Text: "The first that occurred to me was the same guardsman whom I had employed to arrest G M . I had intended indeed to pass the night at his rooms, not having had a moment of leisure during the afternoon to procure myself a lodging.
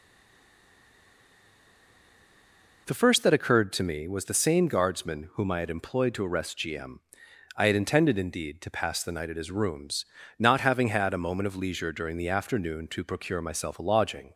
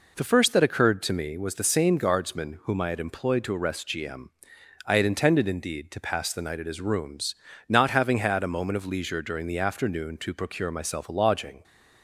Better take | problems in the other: second | stays silent before the first word; strong; until 2.8 s; 2.8 s long

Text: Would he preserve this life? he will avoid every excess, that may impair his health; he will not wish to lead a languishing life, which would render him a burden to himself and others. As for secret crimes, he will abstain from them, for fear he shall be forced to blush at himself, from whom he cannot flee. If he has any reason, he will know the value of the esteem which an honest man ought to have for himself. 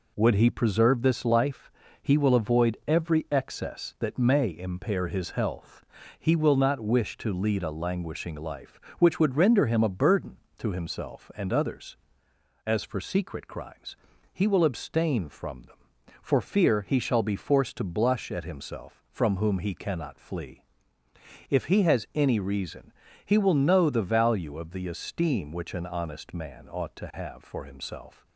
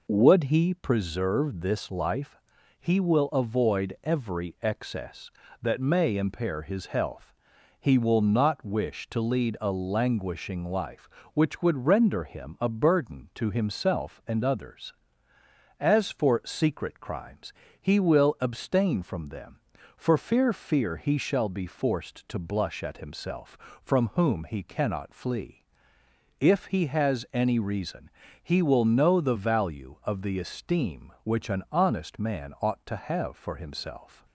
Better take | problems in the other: first | says "fear" twice; at 20.5 s

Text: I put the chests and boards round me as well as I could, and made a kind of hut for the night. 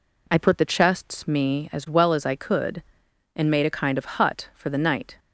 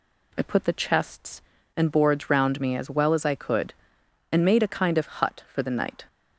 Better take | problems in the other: second | skips "and boards round"; at 1.2 s

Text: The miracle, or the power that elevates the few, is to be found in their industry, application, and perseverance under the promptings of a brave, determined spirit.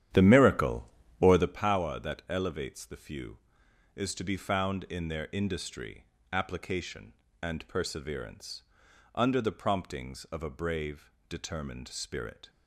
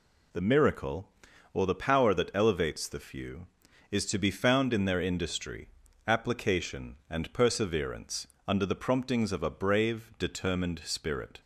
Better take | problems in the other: second | starts louder than the rest; strong; until 1.6 s; 10.5 dB // pauses between "perseverance" and "under"; noticeable; at 8.6 s; 0.52 s long; slight in the second

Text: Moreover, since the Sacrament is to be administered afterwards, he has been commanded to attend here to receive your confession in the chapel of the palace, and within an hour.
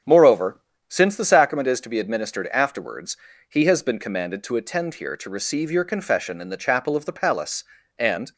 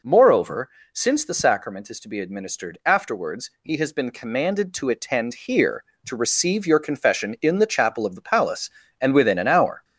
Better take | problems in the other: second | starts louder than the rest; strong; until 1.3 s; 7.5 dB // stops before "within an hour"; at 8.3 s

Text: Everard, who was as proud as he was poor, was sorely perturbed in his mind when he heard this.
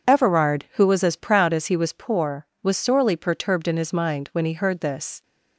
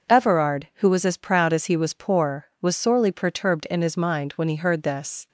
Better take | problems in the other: neither | none

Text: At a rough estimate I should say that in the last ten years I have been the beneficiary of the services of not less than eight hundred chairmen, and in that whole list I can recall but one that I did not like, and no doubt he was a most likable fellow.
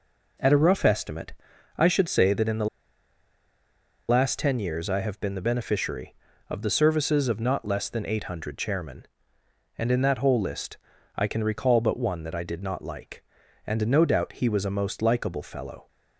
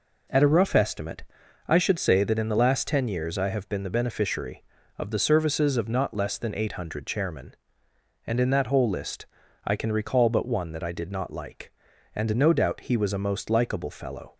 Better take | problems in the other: second | pauses between "estimate" and "I"; noticeable; at 1.3 s; 0.46 s long; noticeable in the second // pauses between "the" and "last"; strong; at 2.6 s; 1.4 s long // pauses between "list" and "I"; at 10.7 s; 0.38 s long; also in the second

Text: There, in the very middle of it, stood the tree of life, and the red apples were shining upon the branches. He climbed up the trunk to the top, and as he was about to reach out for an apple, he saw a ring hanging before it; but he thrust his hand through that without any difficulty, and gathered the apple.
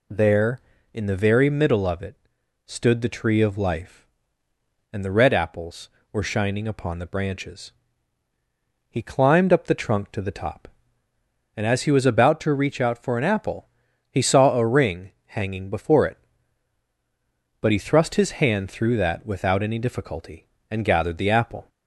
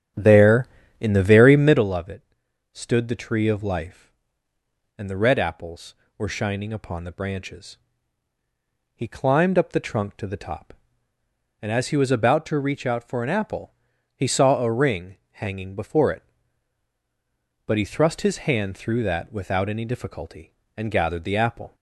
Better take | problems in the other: first | starts louder than the rest; strong; until 1.9 s; 10 dB

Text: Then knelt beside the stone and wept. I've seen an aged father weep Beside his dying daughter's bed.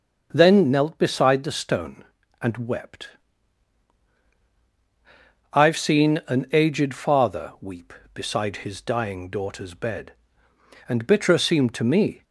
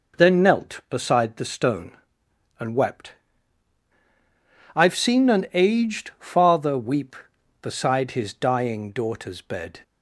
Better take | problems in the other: second | starts louder than the rest; until 1.3 s; 6.5 dB // goes on to say "And bitterer seemed to me"; from 10.8 s on; 1.3 s long

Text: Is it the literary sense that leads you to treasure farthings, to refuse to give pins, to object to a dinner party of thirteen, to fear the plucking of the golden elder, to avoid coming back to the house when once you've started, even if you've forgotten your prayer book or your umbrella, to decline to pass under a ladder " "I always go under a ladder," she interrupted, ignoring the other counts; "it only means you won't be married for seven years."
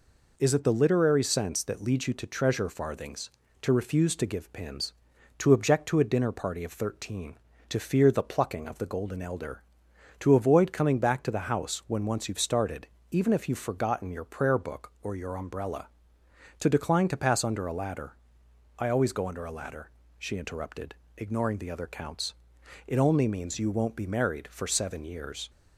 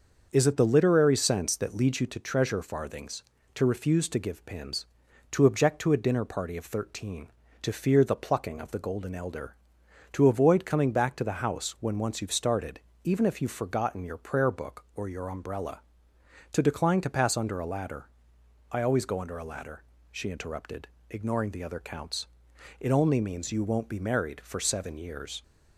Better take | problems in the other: first | starts louder than the rest; until 2.2 s; 6.5 dB

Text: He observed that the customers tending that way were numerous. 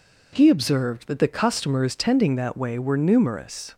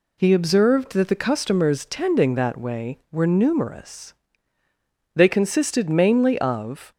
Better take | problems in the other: first | goes on to say "They consisted mainly of"; strong; from 5.1 s on; 1.7 s long

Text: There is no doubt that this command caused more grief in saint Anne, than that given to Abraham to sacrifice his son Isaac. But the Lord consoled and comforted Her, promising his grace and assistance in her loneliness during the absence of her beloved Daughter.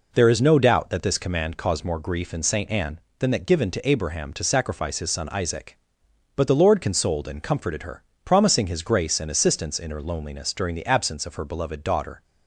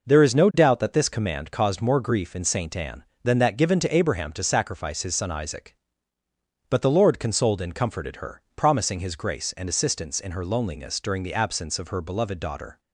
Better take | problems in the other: neither | none

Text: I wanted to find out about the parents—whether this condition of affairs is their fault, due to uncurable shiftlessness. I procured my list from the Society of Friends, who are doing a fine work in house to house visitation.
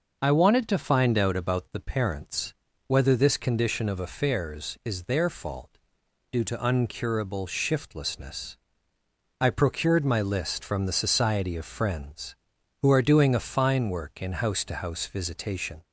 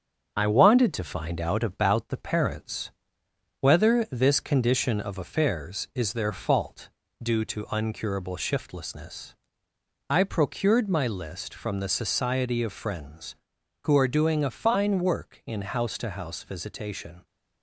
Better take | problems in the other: first | gets quieter; throughout; 3.5 dB

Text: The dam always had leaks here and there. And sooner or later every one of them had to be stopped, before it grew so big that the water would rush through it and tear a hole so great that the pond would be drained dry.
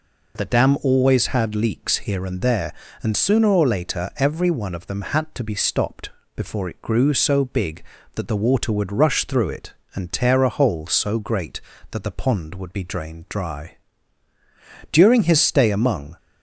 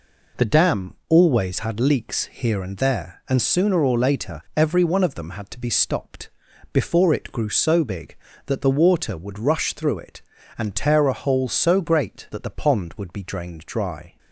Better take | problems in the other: second | goes on to say "During his stay among"; noticeable; from 14.9 s on; 1.2 s long

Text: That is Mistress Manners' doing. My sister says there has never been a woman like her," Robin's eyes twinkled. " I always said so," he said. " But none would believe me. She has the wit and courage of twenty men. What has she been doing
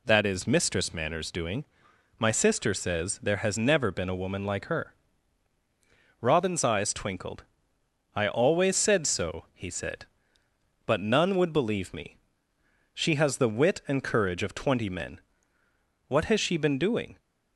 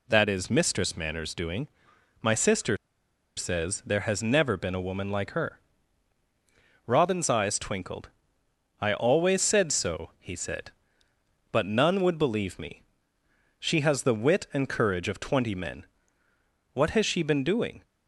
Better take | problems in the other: first | pauses between "sister" and "says"; noticeable; at 2.7 s; 0.60 s long

